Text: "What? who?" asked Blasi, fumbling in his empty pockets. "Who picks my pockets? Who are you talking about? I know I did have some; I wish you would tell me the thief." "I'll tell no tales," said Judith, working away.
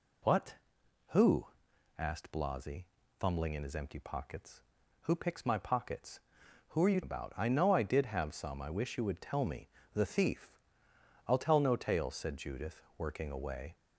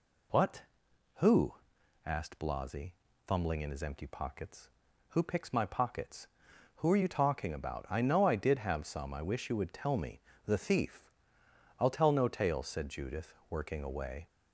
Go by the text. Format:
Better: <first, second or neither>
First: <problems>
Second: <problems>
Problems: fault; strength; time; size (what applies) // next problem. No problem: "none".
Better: second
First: skips "talking"; at 7.0 s // pauses between "me" and "the"; slight; at 9.6 s; 0.26 s long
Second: pauses between "me" and "the"; slight; at 10.1 s; 0.26 s long